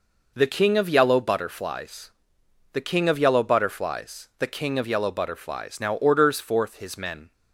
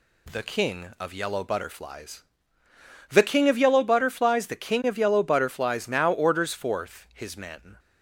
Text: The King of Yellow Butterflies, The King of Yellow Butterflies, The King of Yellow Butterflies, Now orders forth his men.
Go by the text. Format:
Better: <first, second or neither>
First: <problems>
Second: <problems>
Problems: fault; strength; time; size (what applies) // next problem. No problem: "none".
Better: neither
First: none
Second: none